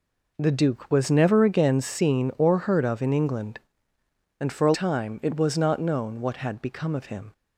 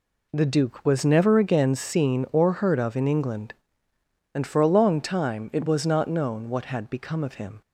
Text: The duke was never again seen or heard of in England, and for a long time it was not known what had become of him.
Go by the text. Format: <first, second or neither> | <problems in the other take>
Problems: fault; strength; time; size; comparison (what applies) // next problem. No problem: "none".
second | skips "long"; at 4.7 s